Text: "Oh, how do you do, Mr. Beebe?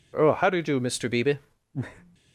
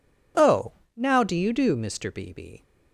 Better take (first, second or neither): first